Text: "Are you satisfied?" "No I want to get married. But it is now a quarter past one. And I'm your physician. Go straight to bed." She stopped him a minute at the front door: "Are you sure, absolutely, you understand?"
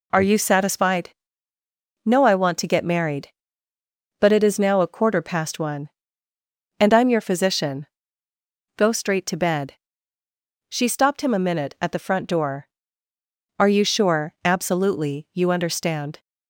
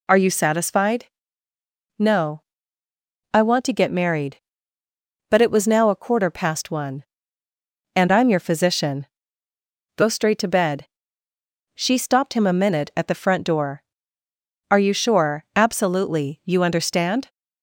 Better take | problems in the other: first | pauses between "No" and "I"; noticeable; at 2.4 s; 0.94 s long // says "was" for "is"; at 5.4 s

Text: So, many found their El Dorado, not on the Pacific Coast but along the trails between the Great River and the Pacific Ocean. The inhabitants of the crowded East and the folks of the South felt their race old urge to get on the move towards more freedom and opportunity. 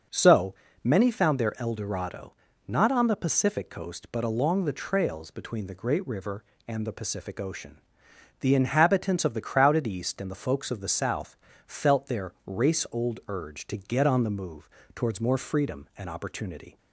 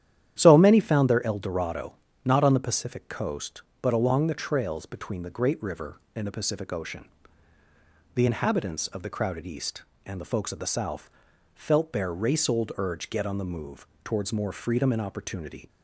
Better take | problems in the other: first | starts louder than the rest; strong; until 1.3 s; 10.5 dB // pauses between "South" and "felt"; at 11.1 s; 0.44 s long; slight in the first // skips "to"; at 13.1 s // pauses between "move" and "towards"; slight; at 13.8 s; 0.16 s long; slight in the first

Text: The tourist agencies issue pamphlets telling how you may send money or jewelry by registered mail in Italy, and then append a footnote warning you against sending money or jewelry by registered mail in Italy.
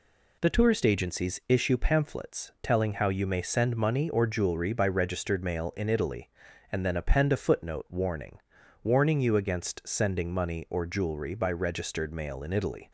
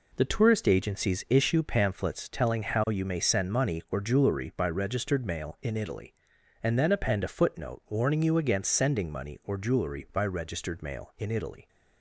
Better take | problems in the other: second | says "warning" twice; at 8.8 s

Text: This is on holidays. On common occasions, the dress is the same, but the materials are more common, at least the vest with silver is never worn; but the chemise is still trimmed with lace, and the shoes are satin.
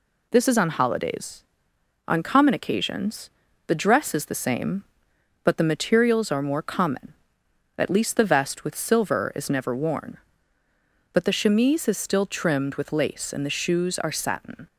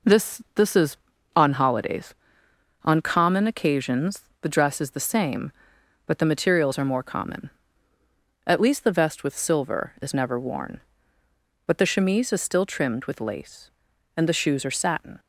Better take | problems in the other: first | says "This" twice; at 0.5 s

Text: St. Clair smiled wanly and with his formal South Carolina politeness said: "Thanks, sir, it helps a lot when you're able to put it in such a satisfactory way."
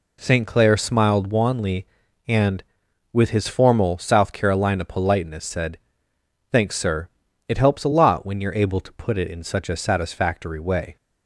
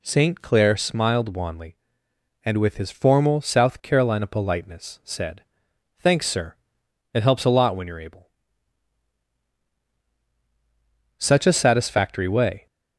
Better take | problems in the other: first | skips "to put it in"; at 9.7 s

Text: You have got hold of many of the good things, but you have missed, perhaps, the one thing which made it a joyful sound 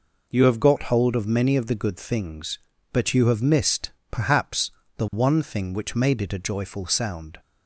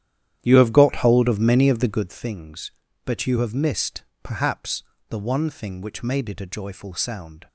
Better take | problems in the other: first | starts louder than the rest; strong; until 2.2 s; 10.5 dB

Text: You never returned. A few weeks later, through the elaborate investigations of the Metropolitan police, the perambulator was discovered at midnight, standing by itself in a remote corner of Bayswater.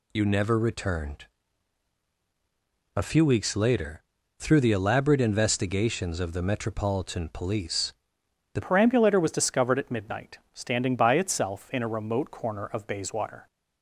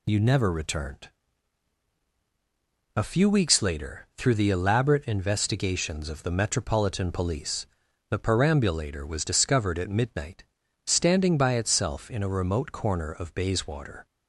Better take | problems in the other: second | changes voice at "perambulator"; from 8.6 s on; 4.8 s long

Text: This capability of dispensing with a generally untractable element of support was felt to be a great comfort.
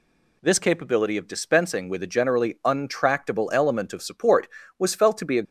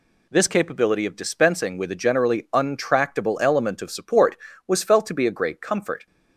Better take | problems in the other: second | stops before "great comfort"; at 5.4 s

